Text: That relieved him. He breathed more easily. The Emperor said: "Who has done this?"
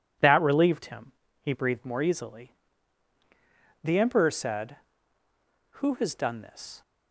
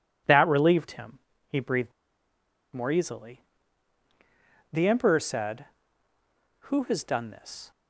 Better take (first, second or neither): first